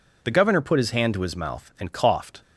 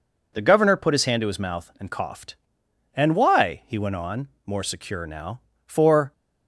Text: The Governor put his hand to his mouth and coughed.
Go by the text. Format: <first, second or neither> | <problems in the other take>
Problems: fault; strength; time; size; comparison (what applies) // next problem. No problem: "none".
first | goes on to say "And why he went on more secure now for"; strong; from 2.9 s on; 3.1 s long